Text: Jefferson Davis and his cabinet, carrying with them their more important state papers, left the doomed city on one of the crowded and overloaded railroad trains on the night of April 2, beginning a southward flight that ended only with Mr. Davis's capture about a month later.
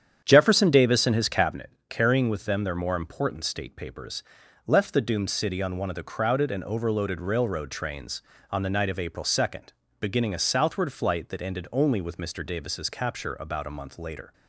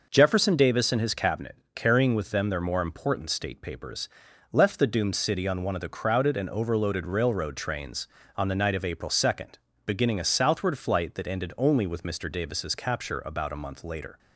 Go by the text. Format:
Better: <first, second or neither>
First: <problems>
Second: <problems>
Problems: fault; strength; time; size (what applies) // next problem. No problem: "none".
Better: second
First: starts louder than the rest; strong; until 1.7 s; 8.5 dB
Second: none